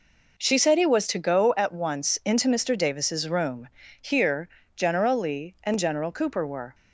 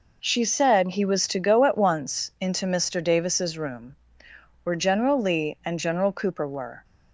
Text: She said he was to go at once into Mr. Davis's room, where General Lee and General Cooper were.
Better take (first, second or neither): second